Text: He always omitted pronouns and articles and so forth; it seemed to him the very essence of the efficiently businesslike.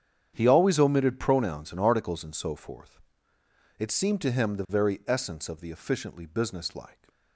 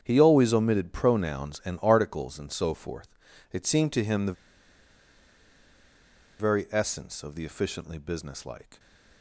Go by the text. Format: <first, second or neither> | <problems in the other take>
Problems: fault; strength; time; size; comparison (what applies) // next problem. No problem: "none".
first | starts louder than the rest; strong; until 1.0 s; 8 dB; strong in the first // pauses between "the" and "very"; strong; at 4.3 s; 2.0 s long